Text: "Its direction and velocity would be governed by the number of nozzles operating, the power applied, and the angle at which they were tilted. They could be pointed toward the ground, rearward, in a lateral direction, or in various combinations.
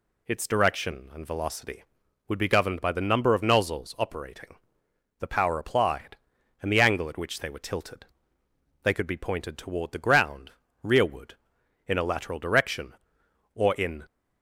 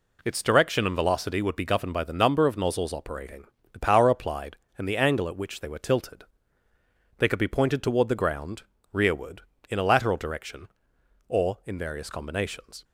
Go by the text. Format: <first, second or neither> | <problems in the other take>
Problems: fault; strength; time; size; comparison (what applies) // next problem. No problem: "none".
second | stops before "various combinations"; at 14.0 s